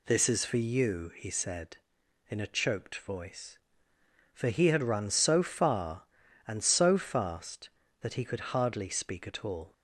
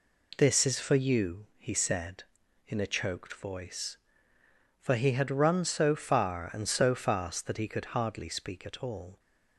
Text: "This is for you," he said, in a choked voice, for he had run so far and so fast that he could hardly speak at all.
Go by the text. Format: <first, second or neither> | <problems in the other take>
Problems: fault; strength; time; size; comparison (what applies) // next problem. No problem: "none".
neither | none